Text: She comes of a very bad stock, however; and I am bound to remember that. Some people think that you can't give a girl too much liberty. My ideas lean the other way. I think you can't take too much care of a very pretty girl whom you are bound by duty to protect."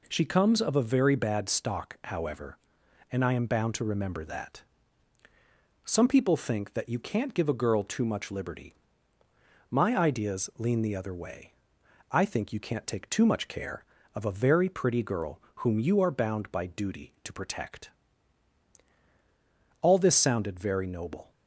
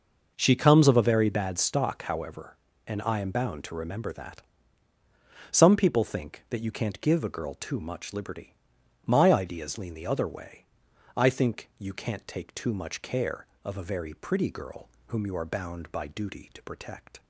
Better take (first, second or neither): second